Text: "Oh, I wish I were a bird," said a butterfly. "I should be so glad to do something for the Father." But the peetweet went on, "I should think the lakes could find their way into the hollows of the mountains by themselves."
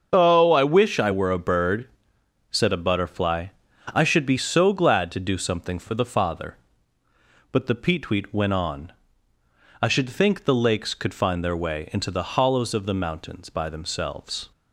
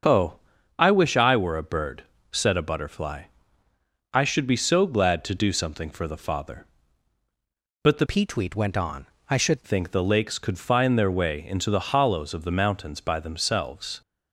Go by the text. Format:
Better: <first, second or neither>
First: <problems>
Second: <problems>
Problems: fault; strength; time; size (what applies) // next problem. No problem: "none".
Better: first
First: starts louder than the rest; until 1.1 s; 7 dB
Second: starts louder than the rest; until 1.4 s; 6.5 dB // changes voice from "peetweet" to "should"; from 8.0 to 9.6 s; 1.6 s long